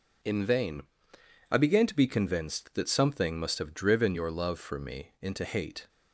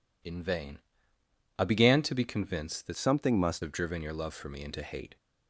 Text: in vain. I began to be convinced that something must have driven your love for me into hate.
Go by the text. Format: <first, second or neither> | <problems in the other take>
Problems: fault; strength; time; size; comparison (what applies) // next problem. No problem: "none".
first | changes voice from "something" to "must"; from 2.9 to 3.6 s; 0.7 s long